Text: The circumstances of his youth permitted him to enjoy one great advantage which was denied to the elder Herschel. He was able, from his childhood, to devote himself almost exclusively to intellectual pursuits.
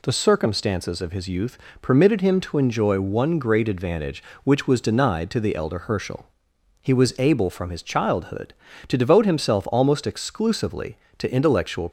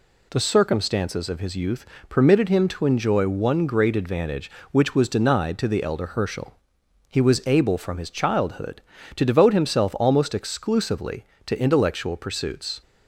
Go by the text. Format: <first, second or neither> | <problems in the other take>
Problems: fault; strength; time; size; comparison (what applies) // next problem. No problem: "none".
second | pauses between "youth" and "permitted"; slight; at 1.5 s; 0.24 s long; slight in the second // stops before "pursuits"; at 11.8 s